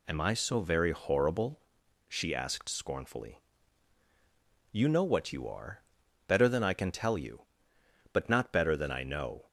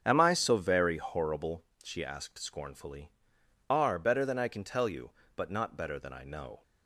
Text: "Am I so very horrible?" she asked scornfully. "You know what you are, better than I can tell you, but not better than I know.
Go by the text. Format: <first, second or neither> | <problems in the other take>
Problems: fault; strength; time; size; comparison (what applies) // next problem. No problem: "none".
first | starts louder than the rest; strong; until 1.0 s; 7.5 dB // skips "You know what you"; at 3.4 s